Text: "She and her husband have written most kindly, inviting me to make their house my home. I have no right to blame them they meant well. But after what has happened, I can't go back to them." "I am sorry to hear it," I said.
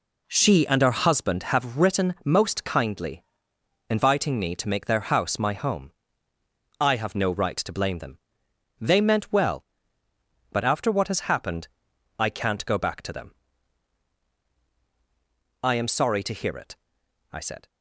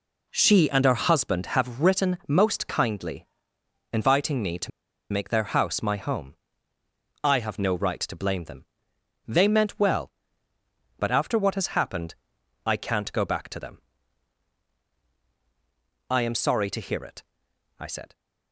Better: first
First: pauses between "them" and "they"; noticeable; at 8.1 s; 0.64 s long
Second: pauses between "to" and "make"; at 4.7 s; 0.42 s long // pauses between "them" and "they"; noticeable; at 8.6 s; 0.64 s long

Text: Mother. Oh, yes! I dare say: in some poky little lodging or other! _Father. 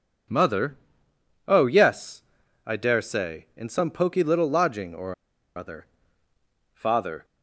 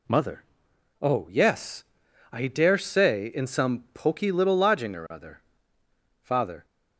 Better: second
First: pauses between "or" and "other"; at 5.1 s; 0.42 s long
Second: none

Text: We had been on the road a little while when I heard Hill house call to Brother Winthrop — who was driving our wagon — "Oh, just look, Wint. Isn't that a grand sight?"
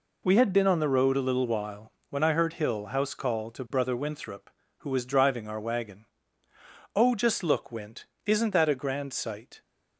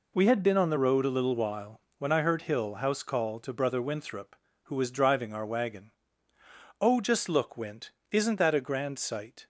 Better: neither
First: pauses between "while" and "when"; slight; at 1.9 s; 0.16 s long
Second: pauses between "while" and "when"; slight; at 1.8 s; 0.16 s long

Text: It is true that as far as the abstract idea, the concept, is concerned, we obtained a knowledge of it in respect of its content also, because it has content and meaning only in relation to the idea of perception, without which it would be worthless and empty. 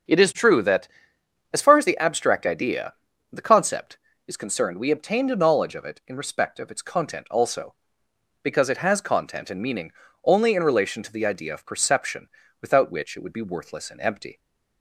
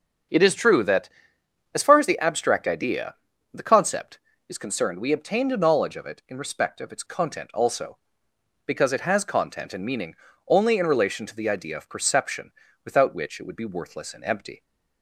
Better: neither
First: starts louder than the rest; until 1.7 s; 7 dB // pauses between "meaning" and "only"; slight; at 9.9 s; 0.32 s long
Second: starts louder than the rest; until 1.9 s; 7 dB // pauses between "meaning" and "only"; slight; at 10.1 s; 0.32 s long

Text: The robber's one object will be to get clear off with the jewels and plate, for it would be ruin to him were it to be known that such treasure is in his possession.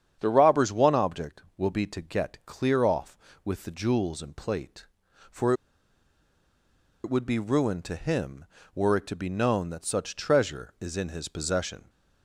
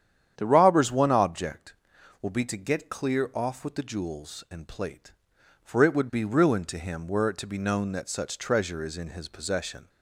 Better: second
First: starts louder than the rest; strong; until 1.1 s; 8.5 dB // pauses between "for" and "it"; strong; at 5.5 s; 1.5 s long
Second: starts louder than the rest; strong; until 1.3 s; 9.5 dB

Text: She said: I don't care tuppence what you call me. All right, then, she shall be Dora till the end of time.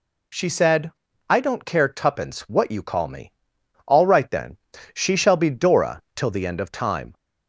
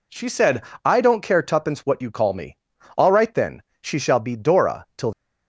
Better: first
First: none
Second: stops before "the end of time"; at 5.1 s

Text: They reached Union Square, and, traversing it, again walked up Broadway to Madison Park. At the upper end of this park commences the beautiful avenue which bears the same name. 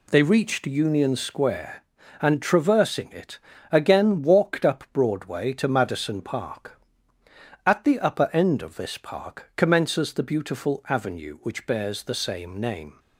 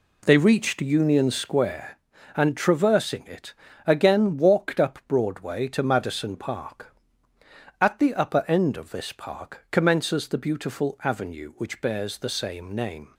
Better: first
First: none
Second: starts louder than the rest; slight; until 1.7 s; 2 dB

